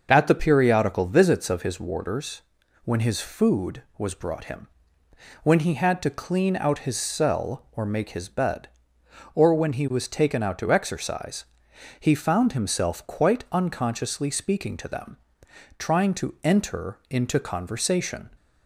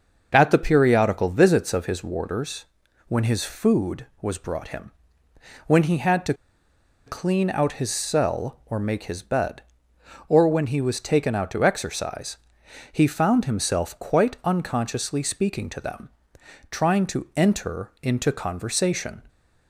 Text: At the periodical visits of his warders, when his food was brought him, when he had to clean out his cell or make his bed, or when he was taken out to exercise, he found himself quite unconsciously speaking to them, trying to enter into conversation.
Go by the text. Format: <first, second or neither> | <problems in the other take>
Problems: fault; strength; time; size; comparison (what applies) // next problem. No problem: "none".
first | starts louder than the rest; until 1.3 s; 6.5 dB; also in the first // pauses between "to" and "clean"; noticeable; at 6.3 s; 0.72 s long